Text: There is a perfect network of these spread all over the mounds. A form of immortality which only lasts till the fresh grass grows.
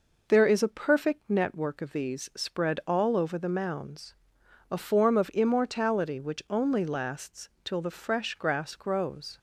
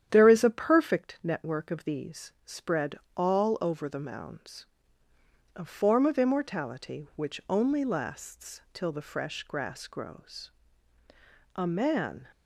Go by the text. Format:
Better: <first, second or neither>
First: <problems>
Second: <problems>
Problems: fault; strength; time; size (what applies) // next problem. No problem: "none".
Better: first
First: none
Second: starts louder than the rest; strong; until 1.1 s; 9.5 dB // pauses between "spread" and "all"; slight; at 2.9 s; 0.20 s long // goes on to say "A man"; noticeable; from 11.5 s on; 0.72 s long